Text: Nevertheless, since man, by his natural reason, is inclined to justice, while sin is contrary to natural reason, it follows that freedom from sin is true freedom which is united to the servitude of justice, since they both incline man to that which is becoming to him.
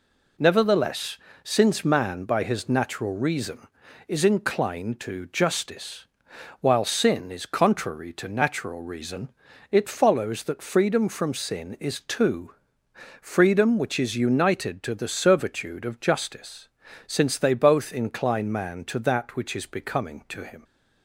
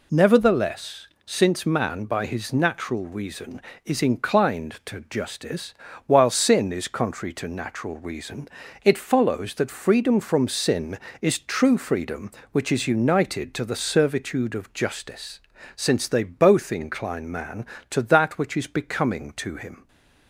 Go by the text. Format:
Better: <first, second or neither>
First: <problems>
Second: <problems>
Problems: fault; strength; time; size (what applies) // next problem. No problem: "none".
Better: second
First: says "two" for "true"; at 12.0 s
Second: none